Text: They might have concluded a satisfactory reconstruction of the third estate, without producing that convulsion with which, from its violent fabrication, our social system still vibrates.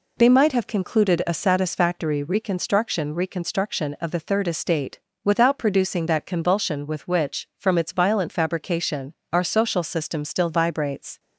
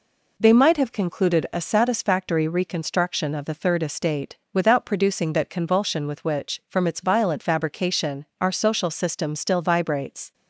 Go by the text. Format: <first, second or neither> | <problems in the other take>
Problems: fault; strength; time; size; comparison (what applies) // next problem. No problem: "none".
second | says "reconstruction" twice; at 3.1 s